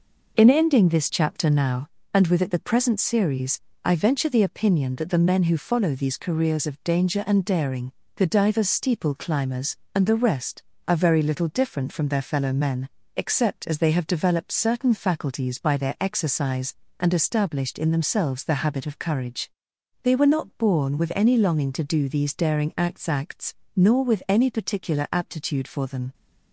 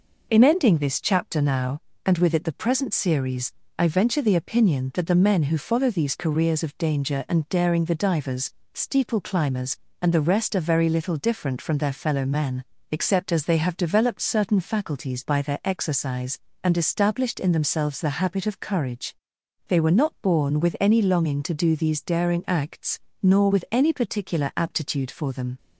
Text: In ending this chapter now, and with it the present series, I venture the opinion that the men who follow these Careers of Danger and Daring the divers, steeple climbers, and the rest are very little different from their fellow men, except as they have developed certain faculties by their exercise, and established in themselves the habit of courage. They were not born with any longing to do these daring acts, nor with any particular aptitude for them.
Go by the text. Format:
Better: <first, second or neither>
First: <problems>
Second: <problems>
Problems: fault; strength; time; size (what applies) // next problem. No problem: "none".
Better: second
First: pauses between "Daring" and "the"; slight; at 7.9 s; 0.24 s long // says "acts" twice; at 23.0 s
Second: none